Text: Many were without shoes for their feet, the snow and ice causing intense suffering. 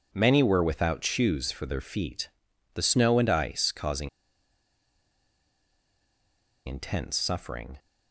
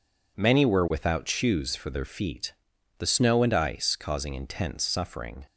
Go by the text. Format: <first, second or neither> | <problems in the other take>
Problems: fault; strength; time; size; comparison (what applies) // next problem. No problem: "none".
second | pauses between "causing" and "intense"; strong; at 4.0 s; 2.5 s long